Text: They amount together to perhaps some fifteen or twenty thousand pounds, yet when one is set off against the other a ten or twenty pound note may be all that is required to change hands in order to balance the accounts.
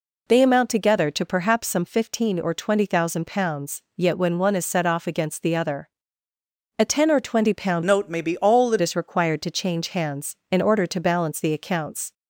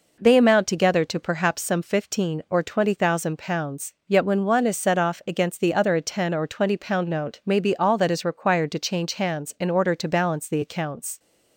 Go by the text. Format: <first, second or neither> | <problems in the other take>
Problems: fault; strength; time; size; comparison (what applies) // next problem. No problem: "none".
second | pauses between "other" and "a"; noticeable; at 5.8 s; 0.90 s long // changes voice from "note" to "that"; from 7.8 to 8.7 s; 0.9 s long